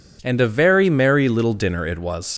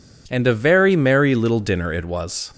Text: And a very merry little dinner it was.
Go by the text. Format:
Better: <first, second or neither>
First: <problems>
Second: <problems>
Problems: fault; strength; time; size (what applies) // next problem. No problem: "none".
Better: second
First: leaves "was" unfinished; at 2.3 s; 90 ms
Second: none